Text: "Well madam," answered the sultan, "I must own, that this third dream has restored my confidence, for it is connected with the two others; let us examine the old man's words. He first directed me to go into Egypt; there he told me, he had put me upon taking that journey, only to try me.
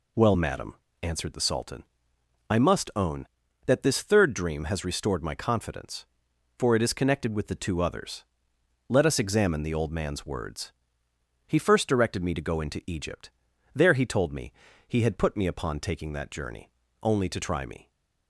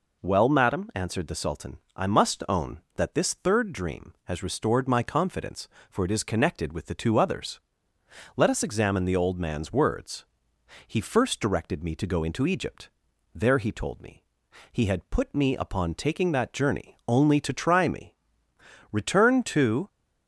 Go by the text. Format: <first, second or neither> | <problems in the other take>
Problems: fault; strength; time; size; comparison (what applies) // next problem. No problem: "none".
first | goes on to say "Return to"; noticeable; from 18.9 s on; 0.96 s long